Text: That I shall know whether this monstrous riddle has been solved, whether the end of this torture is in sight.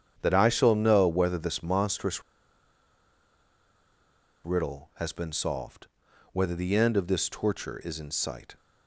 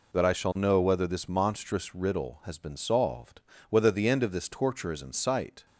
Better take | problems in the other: second | starts louder than the rest; strong; until 1.2 s; 8.5 dB // pauses between "monstrous" and "riddle"; strong; at 2.2 s; 2.2 s long

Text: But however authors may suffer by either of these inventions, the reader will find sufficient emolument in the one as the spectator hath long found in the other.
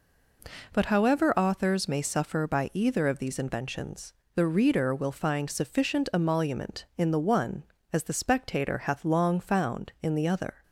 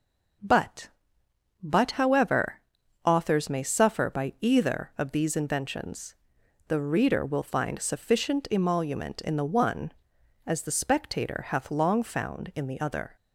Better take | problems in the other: first | says "But" twice; at 1.6 s // pauses between "however" and "authors"; at 2.6 s; 0.44 s long

